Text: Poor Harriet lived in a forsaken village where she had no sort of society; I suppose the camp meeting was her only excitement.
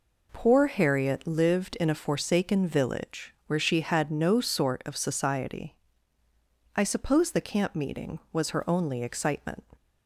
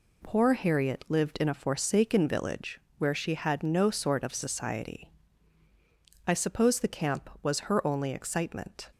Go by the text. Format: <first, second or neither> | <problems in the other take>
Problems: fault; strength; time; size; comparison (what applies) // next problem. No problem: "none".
first | pauses between "village" and "where"; slight; at 2.7 s; 0.18 s long // skips "meeting"; at 7.3 s